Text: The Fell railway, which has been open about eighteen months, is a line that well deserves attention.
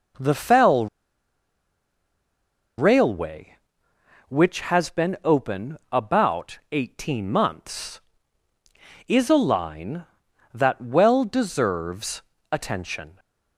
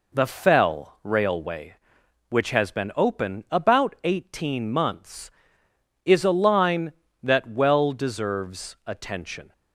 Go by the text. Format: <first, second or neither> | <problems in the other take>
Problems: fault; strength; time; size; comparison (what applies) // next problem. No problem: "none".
second | pauses between "Fell" and "railway"; strong; at 0.8 s; 1.9 s long // pauses between "deserves" and "attention"; slight; at 12.2 s; 0.30 s long